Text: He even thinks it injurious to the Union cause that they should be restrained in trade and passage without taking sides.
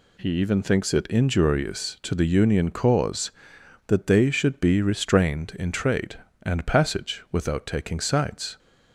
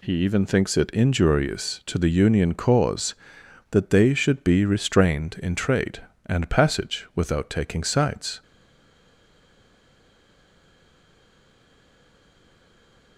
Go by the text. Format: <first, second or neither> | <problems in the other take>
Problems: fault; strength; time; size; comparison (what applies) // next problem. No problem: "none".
first | stays silent after the last word; strong; from 8.4 s on; 4.7 s long